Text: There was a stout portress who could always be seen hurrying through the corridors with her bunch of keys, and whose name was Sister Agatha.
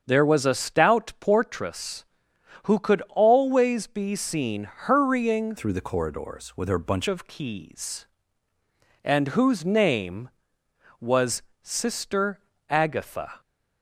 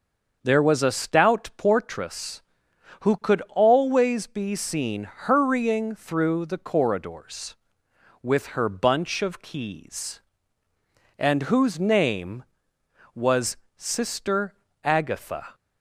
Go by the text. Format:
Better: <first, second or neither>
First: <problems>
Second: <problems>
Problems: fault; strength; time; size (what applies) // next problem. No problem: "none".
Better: second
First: starts louder than the rest; until 1.0 s; 7 dB // changes voice from "through" to "bunch"; from 5.5 to 7.0 s; 1.5 s long // pauses between "was" and "Sister"; slight; at 11.4 s; 0.20 s long // pauses between "Sister" and "Agatha"; slight; at 12.4 s; 0.28 s long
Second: starts louder than the rest; until 1.4 s; 6.5 dB // pauses between "was" and "Sister"; slight; at 13.5 s; 0.20 s long // pauses between "Sister" and "Agatha"; slight; at 14.5 s; 0.28 s long